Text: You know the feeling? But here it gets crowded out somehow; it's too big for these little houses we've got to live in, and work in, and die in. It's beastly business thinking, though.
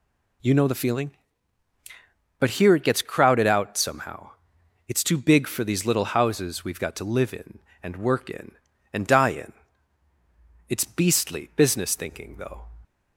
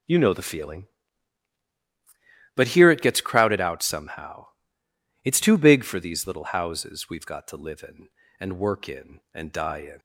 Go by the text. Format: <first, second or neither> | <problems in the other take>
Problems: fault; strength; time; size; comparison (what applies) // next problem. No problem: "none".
first | stops before "It's beastly business thinking though"; at 9.9 s